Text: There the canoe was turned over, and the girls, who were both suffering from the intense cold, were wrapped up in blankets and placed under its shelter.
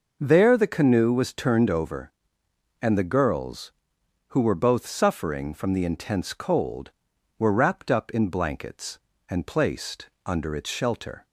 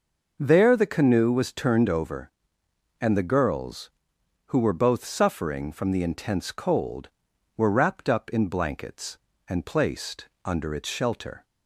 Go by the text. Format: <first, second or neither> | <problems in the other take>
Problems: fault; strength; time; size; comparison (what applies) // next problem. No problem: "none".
neither | none